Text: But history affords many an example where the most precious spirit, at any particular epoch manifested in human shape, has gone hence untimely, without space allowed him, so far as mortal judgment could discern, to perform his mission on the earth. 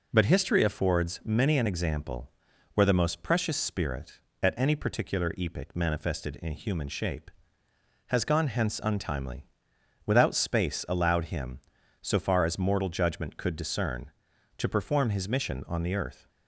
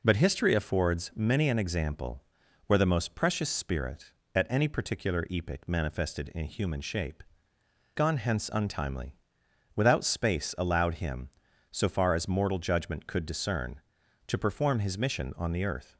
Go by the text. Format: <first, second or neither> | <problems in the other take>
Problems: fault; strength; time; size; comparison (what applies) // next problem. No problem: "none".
first | pauses between "example" and "where"; at 2.2 s; 0.44 s long; also in the first // skips "has"; at 7.5 s